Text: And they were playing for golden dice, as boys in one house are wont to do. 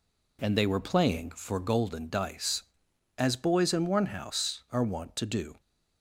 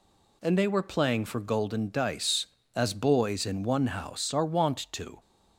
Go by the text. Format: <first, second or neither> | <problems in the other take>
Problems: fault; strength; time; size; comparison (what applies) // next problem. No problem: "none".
first | stops before "do"; at 5.1 s